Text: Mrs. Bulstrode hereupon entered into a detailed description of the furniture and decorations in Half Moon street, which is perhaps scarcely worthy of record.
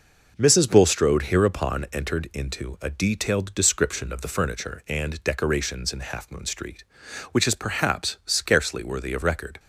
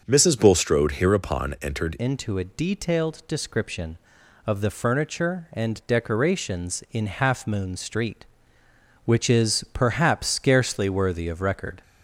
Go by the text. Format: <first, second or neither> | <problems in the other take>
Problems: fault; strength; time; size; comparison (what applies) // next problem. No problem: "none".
first | starts louder than the rest; until 1.0 s; 6.5 dB // changes voice at "into"; from 1.9 s on; 9.9 s long